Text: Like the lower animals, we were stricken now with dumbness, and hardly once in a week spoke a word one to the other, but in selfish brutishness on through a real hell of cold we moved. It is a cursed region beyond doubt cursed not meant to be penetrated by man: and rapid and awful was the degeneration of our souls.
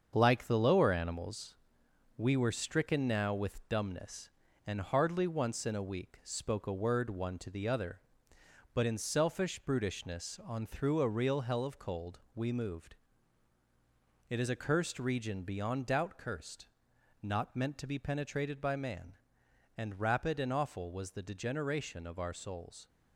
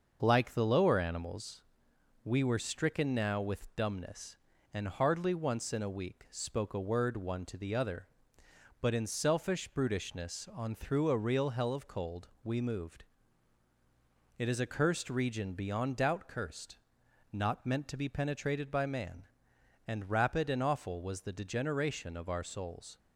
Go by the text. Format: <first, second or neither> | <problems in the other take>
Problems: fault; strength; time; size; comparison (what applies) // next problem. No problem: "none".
second | gets quieter; noticeable; throughout; 5.5 dB // starts louder than the rest; until 1.1 s; 7 dB; also in the second // pauses between "cold" and "we"; slight; at 12.1 s; 0.16 s long; slight in the second // pauses between "cursed" and "not"; noticeable; at 16.6 s; 0.56 s long; noticeable in the second